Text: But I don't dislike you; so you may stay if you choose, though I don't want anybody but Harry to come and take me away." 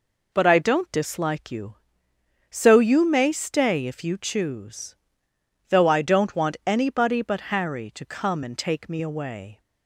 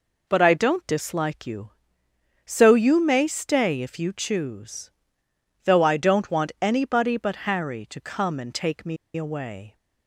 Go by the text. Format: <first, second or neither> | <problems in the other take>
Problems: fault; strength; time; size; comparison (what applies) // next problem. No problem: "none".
first | pauses between "me" and "away"; slight; at 8.9 s; 0.20 s long